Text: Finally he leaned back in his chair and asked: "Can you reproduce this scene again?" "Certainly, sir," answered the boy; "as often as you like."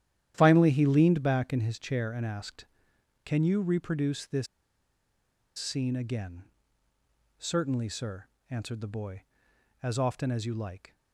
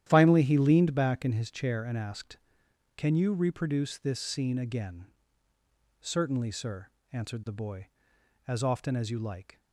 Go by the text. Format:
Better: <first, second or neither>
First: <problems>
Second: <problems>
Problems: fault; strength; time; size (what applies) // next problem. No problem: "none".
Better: second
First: starts louder than the rest; strong; until 1.3 s; 11 dB // pauses between "this" and "scene"; at 4.4 s; 1.1 s long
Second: starts louder than the rest; strong; until 1.1 s; 11 dB